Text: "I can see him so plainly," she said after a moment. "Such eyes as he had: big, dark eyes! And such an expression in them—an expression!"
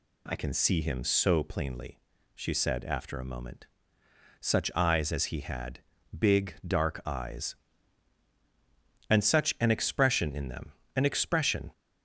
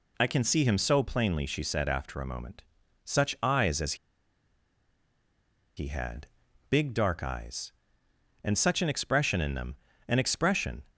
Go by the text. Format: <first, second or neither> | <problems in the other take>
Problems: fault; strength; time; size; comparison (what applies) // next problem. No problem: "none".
first | pauses between "as" and "he"; strong; at 3.9 s; 1.8 s long